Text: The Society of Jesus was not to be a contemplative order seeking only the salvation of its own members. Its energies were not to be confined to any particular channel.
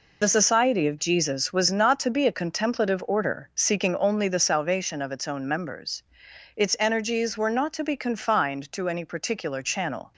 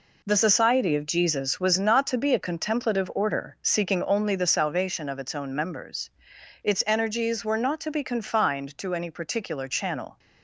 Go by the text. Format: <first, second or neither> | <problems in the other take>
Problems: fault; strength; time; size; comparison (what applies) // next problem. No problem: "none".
second | loses the start of "The"; at 0.2 s; 60 ms